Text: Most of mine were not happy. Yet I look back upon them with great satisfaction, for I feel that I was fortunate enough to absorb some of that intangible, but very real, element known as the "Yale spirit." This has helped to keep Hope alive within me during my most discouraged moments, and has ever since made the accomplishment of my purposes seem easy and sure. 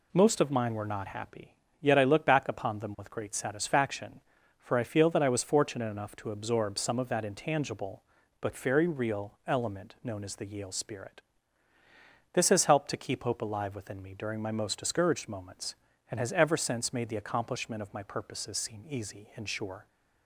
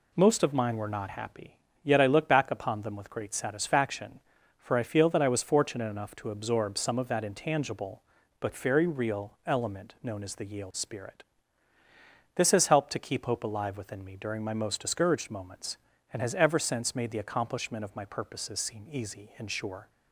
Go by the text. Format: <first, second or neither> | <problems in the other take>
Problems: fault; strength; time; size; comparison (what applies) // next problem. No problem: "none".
neither | none